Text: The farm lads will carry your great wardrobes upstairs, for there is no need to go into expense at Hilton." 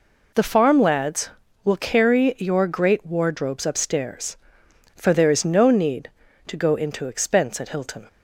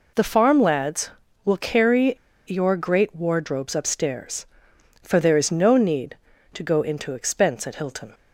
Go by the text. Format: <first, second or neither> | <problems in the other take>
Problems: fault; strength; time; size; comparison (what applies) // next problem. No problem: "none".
first | pauses between "carry" and "your"; slight; at 2.1 s; 0.32 s long